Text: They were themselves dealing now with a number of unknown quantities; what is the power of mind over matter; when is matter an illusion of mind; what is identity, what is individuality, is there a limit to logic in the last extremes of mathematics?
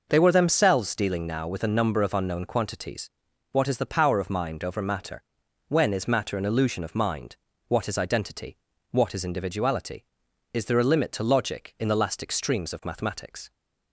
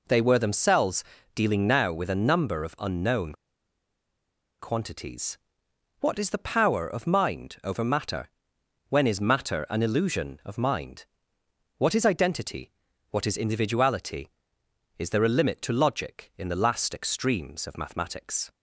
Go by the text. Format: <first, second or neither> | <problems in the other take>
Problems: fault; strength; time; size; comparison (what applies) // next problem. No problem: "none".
first | pauses between "themselves" and "dealing"; slight; at 1.0 s; 0.30 s long // pauses between "unknown" and "quantities"; strong; at 3.3 s; 1.2 s long